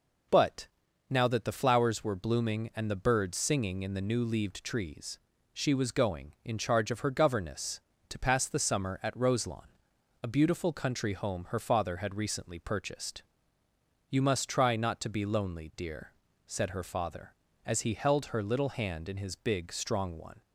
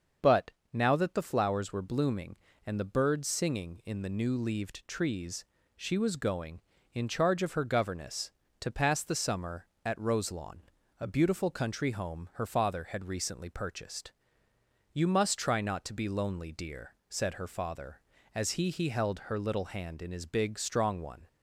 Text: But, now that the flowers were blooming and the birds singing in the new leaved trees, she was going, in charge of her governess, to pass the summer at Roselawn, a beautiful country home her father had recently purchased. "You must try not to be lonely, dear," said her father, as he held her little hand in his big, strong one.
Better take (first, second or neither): first